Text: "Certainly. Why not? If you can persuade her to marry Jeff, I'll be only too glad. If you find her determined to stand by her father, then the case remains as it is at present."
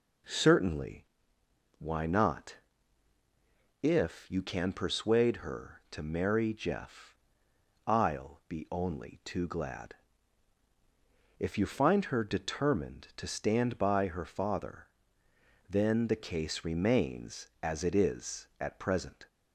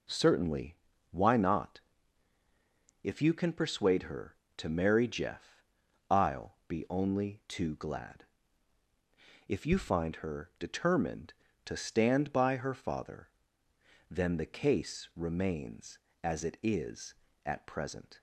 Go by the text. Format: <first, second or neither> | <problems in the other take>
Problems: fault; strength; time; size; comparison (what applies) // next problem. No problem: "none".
neither | none